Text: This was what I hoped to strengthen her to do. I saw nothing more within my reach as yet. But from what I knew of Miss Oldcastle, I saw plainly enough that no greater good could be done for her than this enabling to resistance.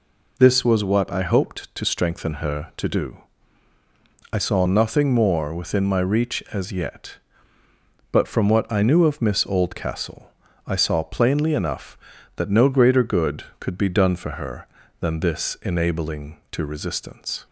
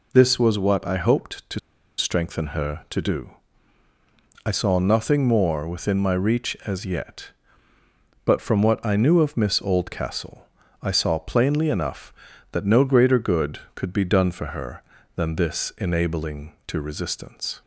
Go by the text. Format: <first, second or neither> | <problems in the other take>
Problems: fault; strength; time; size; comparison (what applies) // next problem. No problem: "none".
first | pauses between "to" and "strengthen"; at 1.5 s; 0.39 s long